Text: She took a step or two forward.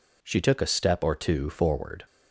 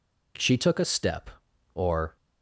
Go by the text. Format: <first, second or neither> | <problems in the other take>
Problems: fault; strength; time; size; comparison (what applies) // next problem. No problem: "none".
first | stops before "two forward"; at 2.1 s